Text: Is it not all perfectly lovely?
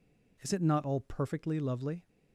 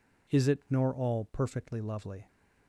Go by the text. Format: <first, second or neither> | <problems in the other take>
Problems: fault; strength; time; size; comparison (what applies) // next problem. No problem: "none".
first | says "nor" for "not"; at 0.6 s